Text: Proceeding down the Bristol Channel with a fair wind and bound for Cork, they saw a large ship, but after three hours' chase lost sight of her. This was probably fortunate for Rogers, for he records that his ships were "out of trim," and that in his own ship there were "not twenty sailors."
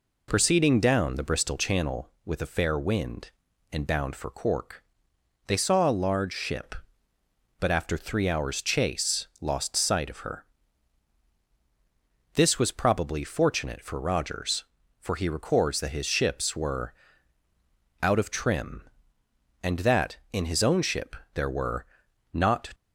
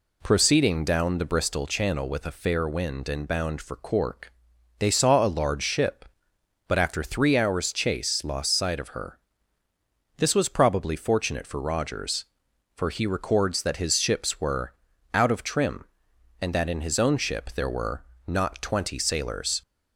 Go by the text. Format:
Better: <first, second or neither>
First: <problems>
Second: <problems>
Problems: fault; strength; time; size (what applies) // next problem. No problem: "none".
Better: second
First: pauses between "were" and "out"; at 16.9 s; 1.1 s long // pauses between "ship" and "there"; slight; at 21.1 s; 0.20 s long // pauses between "were" and "not"; noticeable; at 21.8 s; 0.48 s long // stops before "twenty sailors"; at 22.7 s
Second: pauses between "were" and "out"; at 14.7 s; 0.40 s long // pauses between "were" and "not"; slight; at 18.0 s; 0.24 s long